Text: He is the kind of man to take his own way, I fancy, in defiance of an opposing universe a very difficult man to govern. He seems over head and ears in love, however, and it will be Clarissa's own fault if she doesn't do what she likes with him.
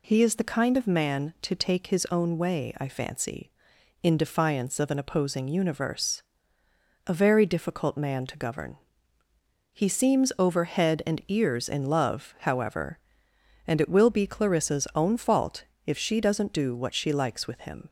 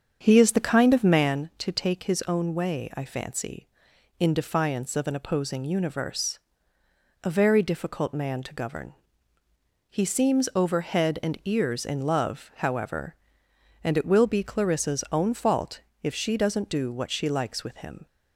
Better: first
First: pauses between "universe" and "a"; noticeable; at 6.2 s; 0.86 s long // pauses between "fault" and "if"; slight; at 15.6 s; 0.22 s long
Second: starts louder than the rest; strong; until 1.4 s; 7 dB // pauses between "universe" and "a"; noticeable; at 6.3 s; 0.86 s long // pauses between "fault" and "if"; slight; at 15.8 s; 0.22 s long

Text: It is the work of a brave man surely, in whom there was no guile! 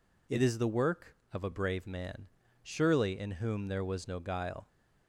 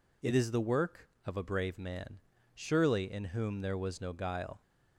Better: neither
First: pauses between "man" and "surely"; slight; at 2.2 s; 0.36 s long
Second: pauses between "man" and "surely"; slight; at 2.1 s; 0.36 s long

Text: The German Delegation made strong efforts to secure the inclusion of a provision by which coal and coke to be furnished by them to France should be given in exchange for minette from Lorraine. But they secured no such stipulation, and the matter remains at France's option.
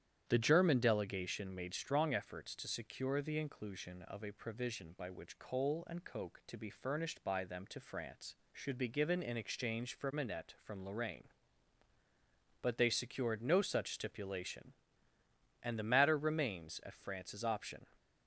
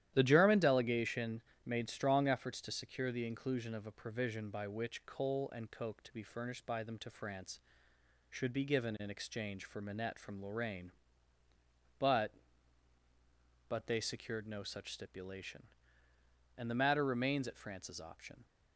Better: first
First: starts louder than the rest; strong; until 1.2 s; 10 dB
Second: starts louder than the rest; strong; until 1.1 s; 12.5 dB // pauses between "Delegation" and "made"; slight; at 1.4 s; 0.24 s long // says "But" twice; at 13.6 s

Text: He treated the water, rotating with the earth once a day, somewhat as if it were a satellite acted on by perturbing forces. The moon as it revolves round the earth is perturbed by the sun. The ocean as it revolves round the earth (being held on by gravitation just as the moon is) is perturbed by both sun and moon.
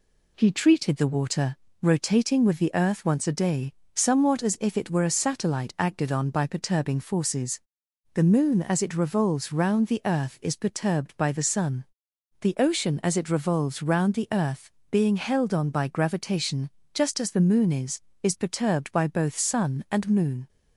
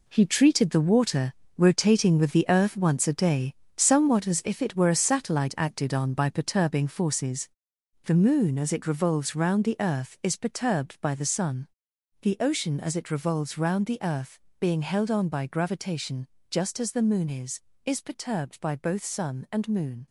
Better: first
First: pauses between "gravitation" and "just"; slight; at 16.7 s; 0.24 s long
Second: gets quieter; strong; throughout; 10 dB // pauses between "gravitation" and "just"; slight; at 16.2 s; 0.20 s long

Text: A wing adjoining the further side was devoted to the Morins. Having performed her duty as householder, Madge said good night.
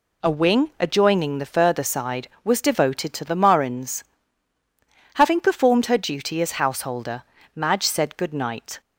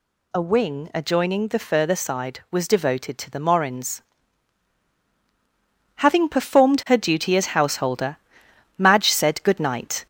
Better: first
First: none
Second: gets louder; slight; throughout; 3 dB

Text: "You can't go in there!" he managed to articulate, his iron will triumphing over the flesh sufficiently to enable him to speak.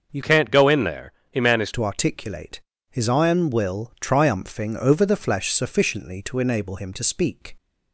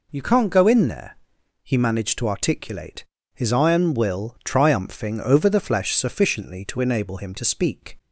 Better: second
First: starts louder than the rest; until 1.1 s; 6.5 dB // changes voice from "can't" to "managed"; from 0.2 to 1.7 s; 1.5 s long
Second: none

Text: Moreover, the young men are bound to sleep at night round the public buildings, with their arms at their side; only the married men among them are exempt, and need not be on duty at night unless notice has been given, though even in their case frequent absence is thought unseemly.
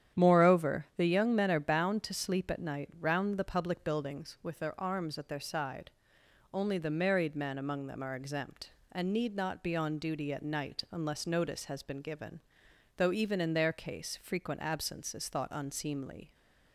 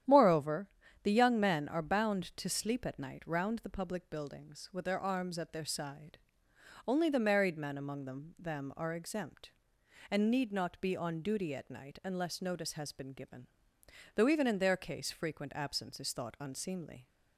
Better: first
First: starts louder than the rest; strong; until 1.2 s; 9.5 dB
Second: starts louder than the rest; strong; until 1.4 s; 10.5 dB // says "them" twice; at 8.3 s

